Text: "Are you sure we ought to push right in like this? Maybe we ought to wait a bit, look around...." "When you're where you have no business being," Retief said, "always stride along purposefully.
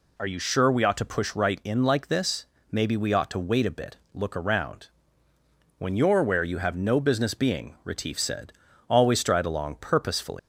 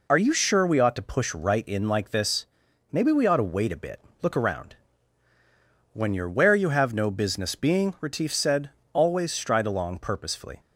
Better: second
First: leaves "purposefully" unfinished; at 10.3 s; 135 ms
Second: none

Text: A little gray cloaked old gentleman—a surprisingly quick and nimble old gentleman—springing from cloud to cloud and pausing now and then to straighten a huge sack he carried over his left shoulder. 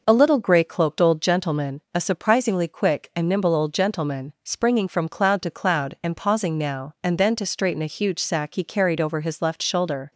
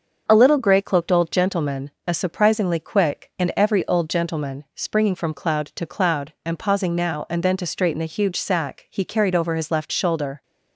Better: first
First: none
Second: starts louder than the rest; until 1.2 s; 6.5 dB // says "every" for "nimble"; at 3.5 s

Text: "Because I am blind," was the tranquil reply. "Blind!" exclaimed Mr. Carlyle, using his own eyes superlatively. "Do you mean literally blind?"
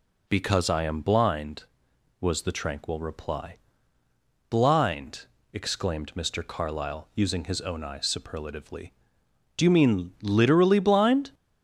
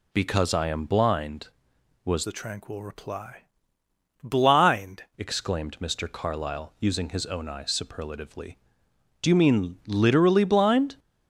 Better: first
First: none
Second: changes voice from "the" to "Blind"; from 2.2 to 5.0 s; 2.8 s long

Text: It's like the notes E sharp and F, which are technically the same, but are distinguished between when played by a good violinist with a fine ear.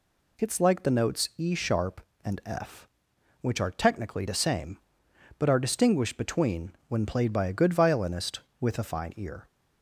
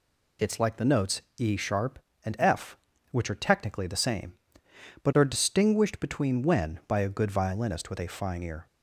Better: first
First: none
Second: pauses between "notes" and "E"; slight; at 1.2 s; 0.18 s long // skips "played"; at 6.8 s

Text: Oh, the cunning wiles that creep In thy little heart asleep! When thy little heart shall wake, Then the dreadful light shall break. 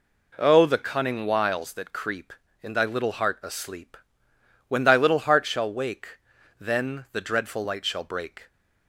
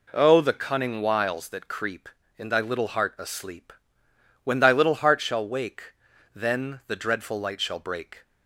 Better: neither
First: none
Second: none

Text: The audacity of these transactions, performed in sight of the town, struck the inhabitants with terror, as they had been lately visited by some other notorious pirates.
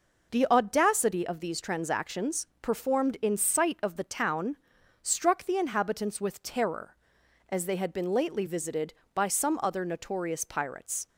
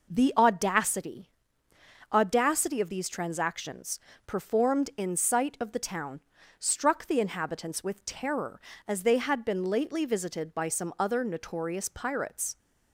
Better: first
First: none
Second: says "audacity" twice; at 2.1 s

